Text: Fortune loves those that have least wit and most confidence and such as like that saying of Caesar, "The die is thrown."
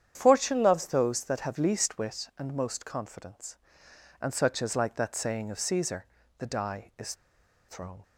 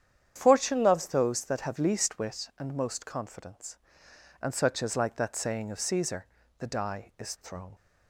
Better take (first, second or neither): second